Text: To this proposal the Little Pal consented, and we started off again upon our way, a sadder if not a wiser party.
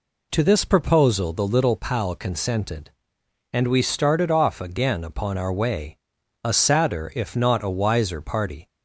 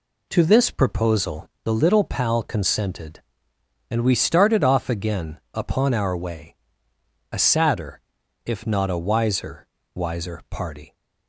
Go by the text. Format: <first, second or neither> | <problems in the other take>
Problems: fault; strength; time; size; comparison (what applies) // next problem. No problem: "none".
first | pauses between "proposal" and "the"; slight; at 1.4 s; 0.16 s long // pauses between "sadder" and "if"; at 7.9 s; 0.45 s long // says "wiser" twice; at 9.9 s